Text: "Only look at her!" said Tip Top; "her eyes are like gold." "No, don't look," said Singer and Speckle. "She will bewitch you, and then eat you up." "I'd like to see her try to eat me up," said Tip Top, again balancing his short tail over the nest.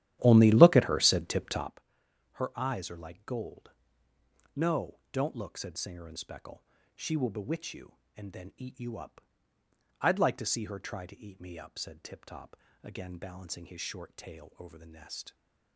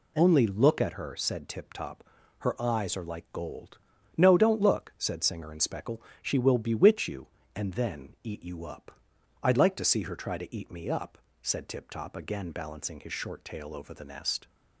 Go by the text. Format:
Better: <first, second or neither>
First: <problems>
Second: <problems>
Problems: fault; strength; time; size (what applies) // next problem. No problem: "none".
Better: second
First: starts louder than the rest; strong; until 1.7 s; 12 dB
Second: none